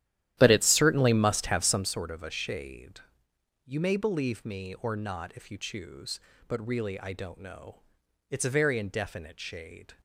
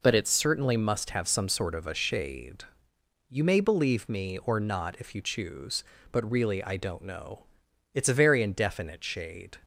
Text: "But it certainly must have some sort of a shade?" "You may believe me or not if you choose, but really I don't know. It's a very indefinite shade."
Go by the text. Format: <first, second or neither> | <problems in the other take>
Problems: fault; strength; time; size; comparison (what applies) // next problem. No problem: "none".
second | starts louder than the rest; strong; until 1.9 s; 12 dB